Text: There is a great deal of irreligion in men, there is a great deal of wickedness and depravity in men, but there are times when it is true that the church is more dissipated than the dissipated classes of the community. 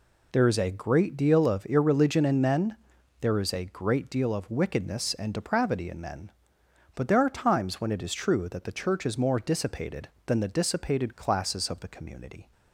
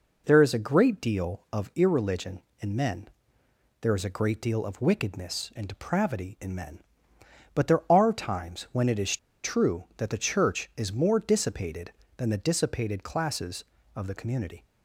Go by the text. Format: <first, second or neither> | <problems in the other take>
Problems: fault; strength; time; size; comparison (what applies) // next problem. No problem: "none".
first | pauses between "is" and "true"; slight; at 9.1 s; 0.25 s long